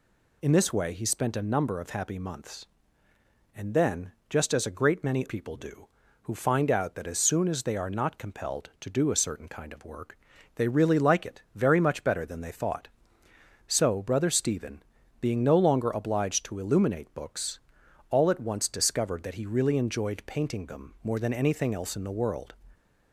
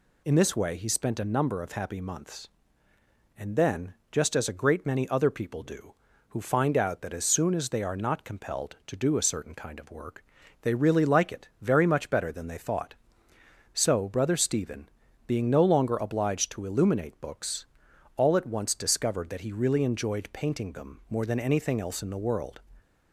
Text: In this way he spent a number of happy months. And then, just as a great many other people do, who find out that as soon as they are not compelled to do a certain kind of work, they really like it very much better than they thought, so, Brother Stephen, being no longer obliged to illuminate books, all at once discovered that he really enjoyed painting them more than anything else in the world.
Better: second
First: skips "other"; at 5.2 s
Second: none

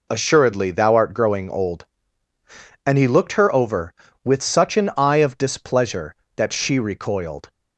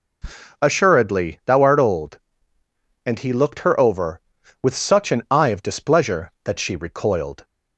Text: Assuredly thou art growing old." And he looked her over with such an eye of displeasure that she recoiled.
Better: first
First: none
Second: skips "growing"; at 1.8 s

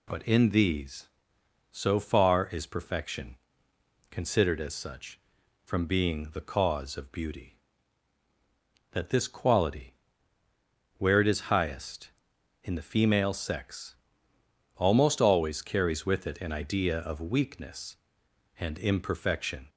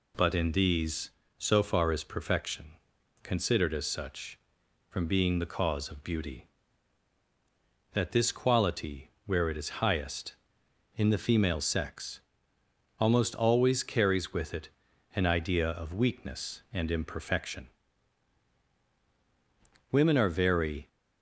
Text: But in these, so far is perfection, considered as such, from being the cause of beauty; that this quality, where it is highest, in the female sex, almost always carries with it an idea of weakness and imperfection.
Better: first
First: none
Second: pauses between "it" and "an"; at 14.6 s; 0.44 s long // goes on to say "Women are very"; noticeable; from 19.9 s on; 0.96 s long

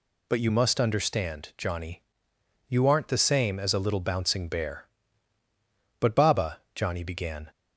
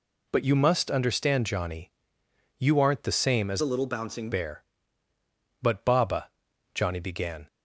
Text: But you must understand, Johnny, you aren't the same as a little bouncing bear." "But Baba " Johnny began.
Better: first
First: none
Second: changes voice from "a" to "bouncing"; from 3.6 to 4.2 s; 0.6 s long

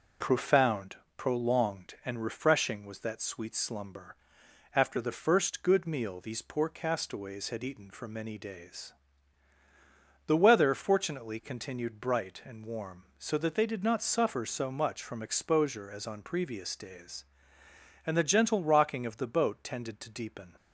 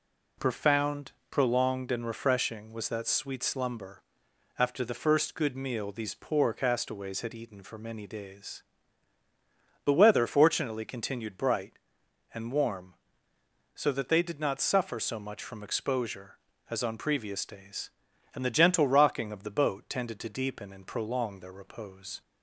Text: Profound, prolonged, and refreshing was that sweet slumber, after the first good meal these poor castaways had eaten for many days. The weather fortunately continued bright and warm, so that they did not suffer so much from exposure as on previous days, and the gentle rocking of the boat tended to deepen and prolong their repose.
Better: second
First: stops before "and prolong their repose"; at 20.5 s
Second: none

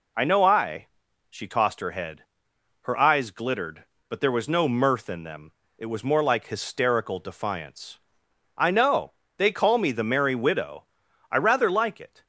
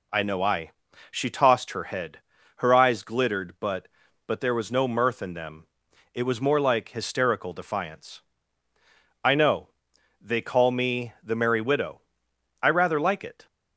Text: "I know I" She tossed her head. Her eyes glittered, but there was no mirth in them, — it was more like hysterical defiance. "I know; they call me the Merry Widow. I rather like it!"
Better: first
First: pauses between "I" and "She"; at 0.8 s; 0.40 s long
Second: pauses between "I" and "She"; at 0.7 s; 0.40 s long // says "but" twice; at 4.2 s

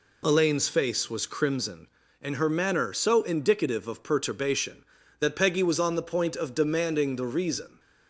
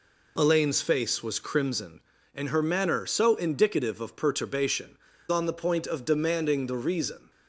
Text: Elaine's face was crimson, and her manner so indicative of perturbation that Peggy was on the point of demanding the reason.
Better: first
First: none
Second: skips "that Peggy was"; at 5.1 s

